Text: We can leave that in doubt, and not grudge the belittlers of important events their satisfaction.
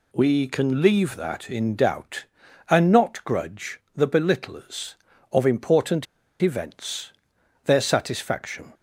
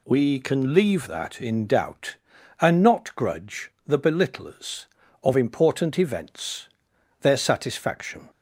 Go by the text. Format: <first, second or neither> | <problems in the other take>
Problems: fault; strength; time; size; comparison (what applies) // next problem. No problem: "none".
second | pauses between "grudge" and "the"; slight; at 3.7 s; 0.16 s long; slight in the second // pauses between "important" and "events"; slight; at 6.0 s; 0.36 s long // pauses between "events" and "their"; noticeable; at 7.1 s; 0.52 s long; noticeable in the second